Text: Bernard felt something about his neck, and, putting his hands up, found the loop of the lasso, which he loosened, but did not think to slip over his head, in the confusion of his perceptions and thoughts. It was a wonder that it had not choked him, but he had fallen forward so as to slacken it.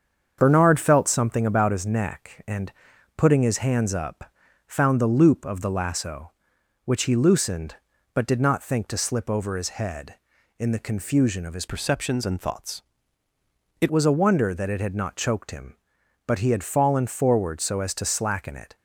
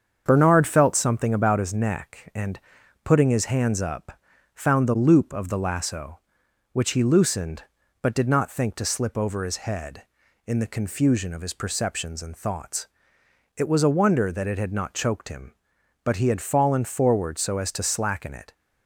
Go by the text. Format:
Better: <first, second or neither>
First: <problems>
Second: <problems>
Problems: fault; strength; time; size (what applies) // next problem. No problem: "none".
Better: second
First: starts louder than the rest; strong; until 1.4 s; 7 dB // changes voice from "perceptions" to "It"; from 11.6 to 13.9 s; 2.3 s long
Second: starts louder than the rest; strong; until 1.2 s; 7 dB